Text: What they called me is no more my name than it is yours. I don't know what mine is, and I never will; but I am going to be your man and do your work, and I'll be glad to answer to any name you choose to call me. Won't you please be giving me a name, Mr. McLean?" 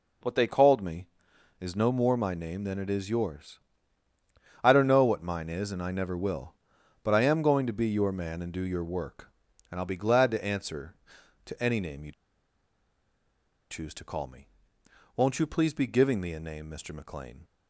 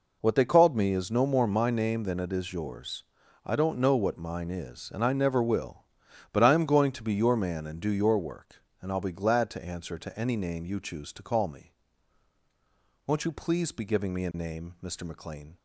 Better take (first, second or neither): second